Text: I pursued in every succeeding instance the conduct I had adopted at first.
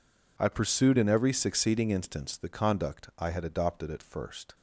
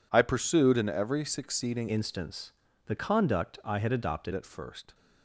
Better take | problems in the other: first | changes voice from "instance" to "adopted"; from 1.8 to 4.3 s; 2.5 s long // pauses between "instance" and "the"; slight; at 2.5 s; 0.34 s long

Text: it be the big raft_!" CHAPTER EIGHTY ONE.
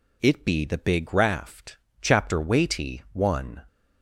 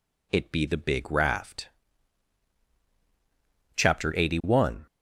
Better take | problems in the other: second | says "Weighty" for "EIGHTY"; at 2.4 s

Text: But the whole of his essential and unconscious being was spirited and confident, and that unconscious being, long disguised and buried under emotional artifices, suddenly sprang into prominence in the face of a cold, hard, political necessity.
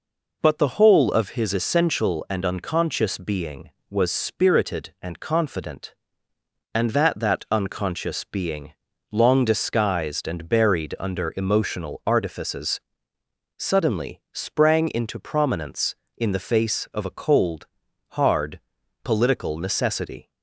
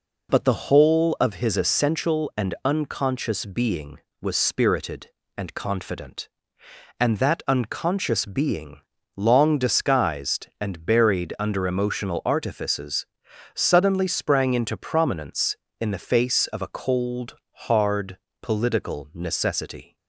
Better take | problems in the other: second | says "that" twice; at 7.1 s

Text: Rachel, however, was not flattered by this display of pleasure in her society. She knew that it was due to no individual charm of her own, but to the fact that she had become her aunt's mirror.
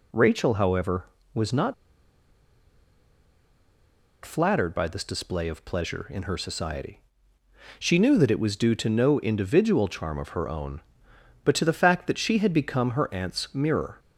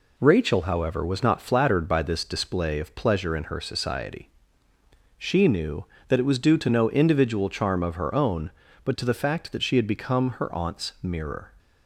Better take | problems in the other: second | pauses between "not" and "flattered"; strong; at 1.7 s; 2.5 s long

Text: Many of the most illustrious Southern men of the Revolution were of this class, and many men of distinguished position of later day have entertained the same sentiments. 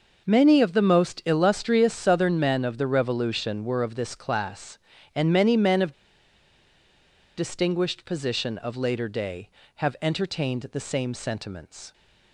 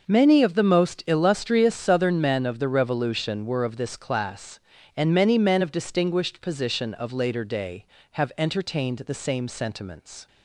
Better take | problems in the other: second | pauses between "of" and "distinguished"; strong; at 5.9 s; 1.4 s long

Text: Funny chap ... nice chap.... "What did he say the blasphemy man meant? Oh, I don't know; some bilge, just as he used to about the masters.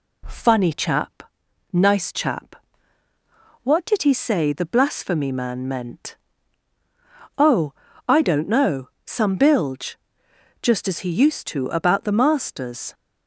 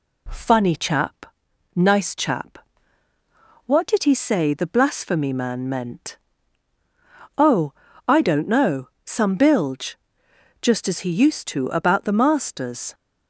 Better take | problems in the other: neither | none

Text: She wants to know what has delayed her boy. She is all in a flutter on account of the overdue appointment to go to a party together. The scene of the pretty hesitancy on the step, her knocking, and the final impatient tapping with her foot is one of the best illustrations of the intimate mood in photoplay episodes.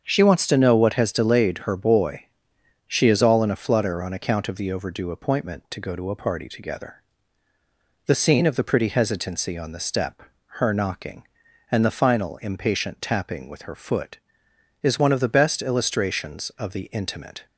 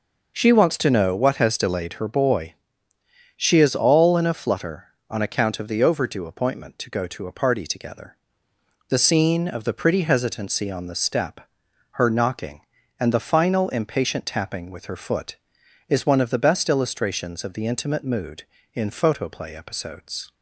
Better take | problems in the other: second | starts louder than the rest; until 1.0 s; 7 dB // stops before "mood in photoplay episodes"; at 17.4 s

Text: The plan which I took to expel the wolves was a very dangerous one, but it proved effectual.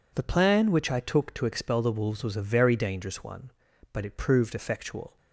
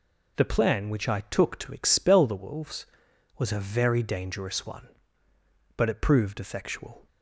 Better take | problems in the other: neither | none

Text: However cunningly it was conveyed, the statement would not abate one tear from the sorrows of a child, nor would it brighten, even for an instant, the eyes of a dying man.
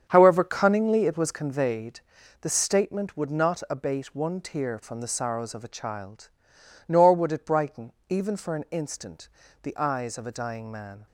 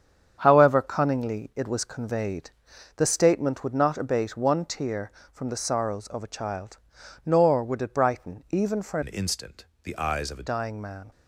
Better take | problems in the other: first | starts louder than the rest; strong; until 1.3 s; 8 dB; strong in the first // changes voice from "an" to "a"; from 9.0 to 10.4 s; 1.4 s long

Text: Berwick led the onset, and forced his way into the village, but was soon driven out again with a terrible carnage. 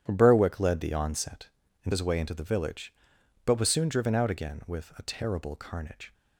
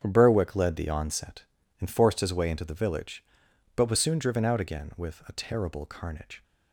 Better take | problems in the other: second | starts louder than the rest; strong; until 1.0 s; 9.5 dB; strong in the second // skips "forced"; at 1.9 s

